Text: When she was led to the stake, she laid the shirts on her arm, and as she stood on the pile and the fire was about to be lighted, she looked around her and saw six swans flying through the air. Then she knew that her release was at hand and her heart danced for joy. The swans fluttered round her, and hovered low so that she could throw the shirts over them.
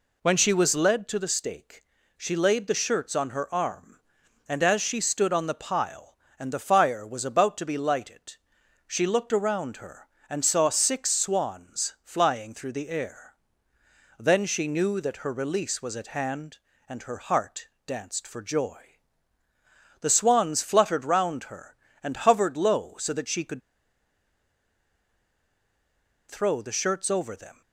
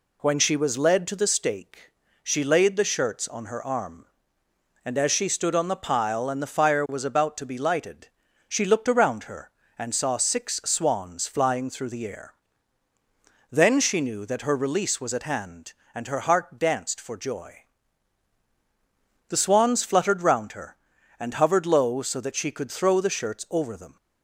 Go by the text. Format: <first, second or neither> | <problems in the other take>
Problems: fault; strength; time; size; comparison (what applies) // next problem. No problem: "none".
second | pauses between "heart" and "danced"; slight; at 17.6 s; 0.18 s long // pauses between "could" and "throw"; strong; at 23.6 s; 2.6 s long